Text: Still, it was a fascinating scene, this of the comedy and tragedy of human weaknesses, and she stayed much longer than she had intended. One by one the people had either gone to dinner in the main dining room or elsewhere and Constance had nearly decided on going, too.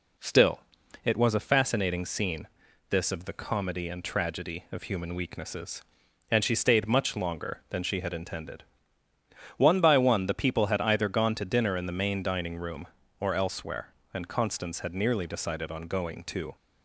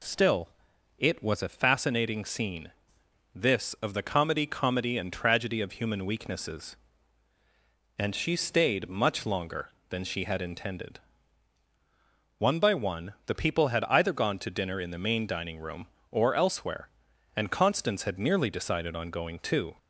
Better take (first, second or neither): first